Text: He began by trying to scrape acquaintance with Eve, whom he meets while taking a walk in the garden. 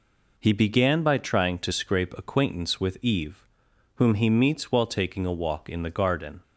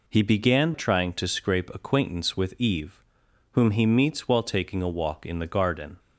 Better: first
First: none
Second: skips "by"; at 0.7 s

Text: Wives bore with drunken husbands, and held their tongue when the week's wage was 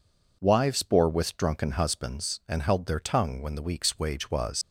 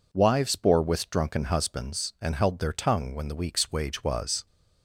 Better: second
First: leaves "was" unfinished; at 4.6 s; 110 ms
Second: none

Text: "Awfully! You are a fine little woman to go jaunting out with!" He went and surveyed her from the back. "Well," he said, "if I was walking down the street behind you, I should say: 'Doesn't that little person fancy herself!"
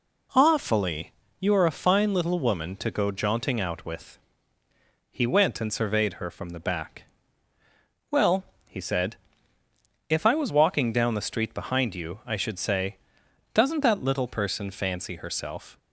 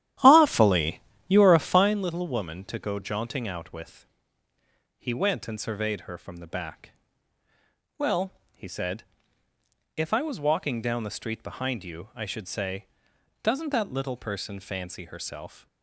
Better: first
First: none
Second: starts louder than the rest; strong; until 2.0 s; 12 dB

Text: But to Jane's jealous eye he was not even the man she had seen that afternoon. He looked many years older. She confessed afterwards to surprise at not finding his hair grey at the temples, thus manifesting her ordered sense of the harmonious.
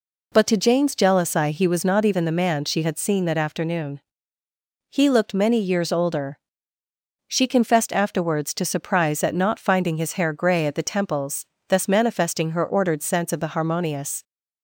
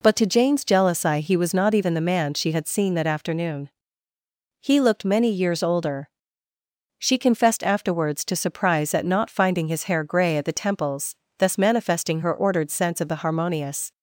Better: neither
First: none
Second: none

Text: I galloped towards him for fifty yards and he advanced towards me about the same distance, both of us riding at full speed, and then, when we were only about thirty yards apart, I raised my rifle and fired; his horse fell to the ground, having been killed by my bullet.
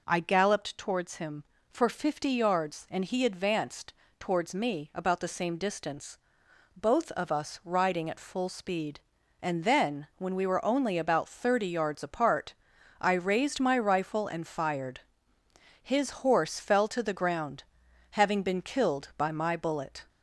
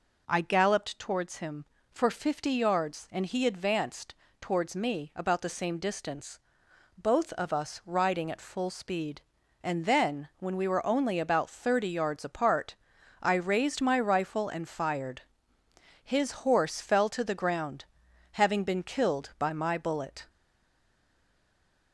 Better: first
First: pauses between "advanced" and "towards"; slight; at 3.9 s; 0.26 s long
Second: pauses between "advanced" and "towards"; slight; at 4.1 s; 0.26 s long // stays silent after the last word; noticeable; from 20.2 s on; 1.7 s long

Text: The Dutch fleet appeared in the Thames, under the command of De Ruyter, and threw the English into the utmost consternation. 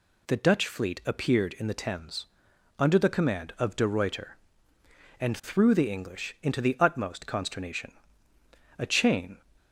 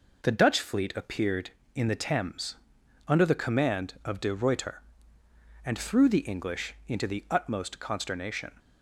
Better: second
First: goes on to say "A chain"; noticeable; from 8.7 s on; 0.62 s long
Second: none

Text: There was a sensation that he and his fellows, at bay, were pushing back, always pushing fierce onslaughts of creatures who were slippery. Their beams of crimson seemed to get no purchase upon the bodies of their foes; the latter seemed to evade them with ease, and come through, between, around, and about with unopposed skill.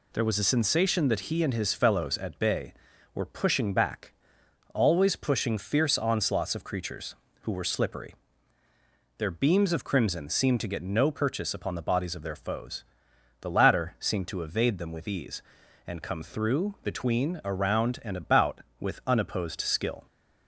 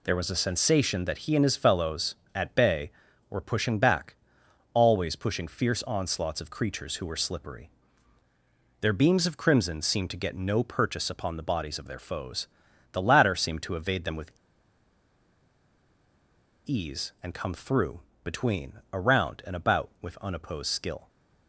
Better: first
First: none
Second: pauses between "with" and "ease"; strong; at 14.3 s; 2.3 s long

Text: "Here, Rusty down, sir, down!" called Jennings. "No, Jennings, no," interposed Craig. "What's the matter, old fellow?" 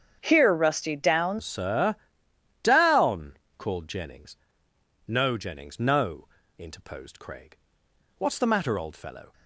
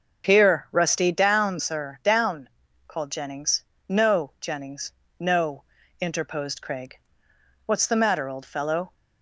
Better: second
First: starts louder than the rest; strong; until 1.2 s; 8 dB // changes voice at "sir"; from 1.4 s on; 7.9 s long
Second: starts louder than the rest; until 1.3 s; 6.5 dB

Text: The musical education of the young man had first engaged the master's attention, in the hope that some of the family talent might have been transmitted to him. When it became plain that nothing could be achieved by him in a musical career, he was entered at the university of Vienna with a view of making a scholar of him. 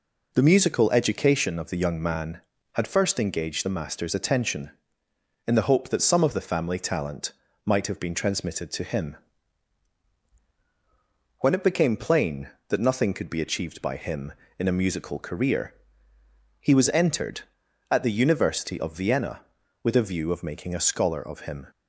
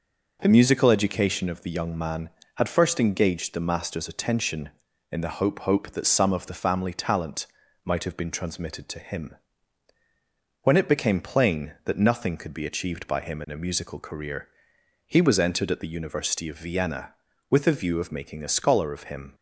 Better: first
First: pauses between "talent" and "might"; slight; at 7.3 s; 0.32 s long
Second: says "hope" twice; at 5.6 s // pauses between "talent" and "might"; at 7.4 s; 0.40 s long

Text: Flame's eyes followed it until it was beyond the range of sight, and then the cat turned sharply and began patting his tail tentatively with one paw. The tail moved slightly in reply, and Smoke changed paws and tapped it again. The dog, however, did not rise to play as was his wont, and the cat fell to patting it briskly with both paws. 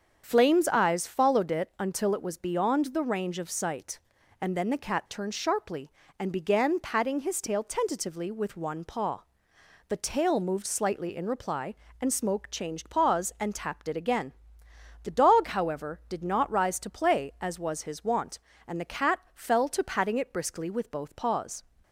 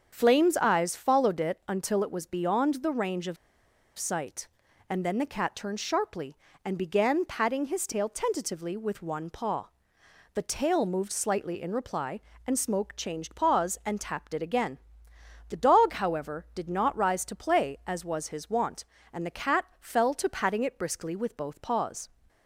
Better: first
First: starts louder than the rest; until 1.2 s; 7 dB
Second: starts louder than the rest; until 1.1 s; 7 dB // pauses between "of" and "sight"; noticeable; at 3.3 s; 0.62 s long

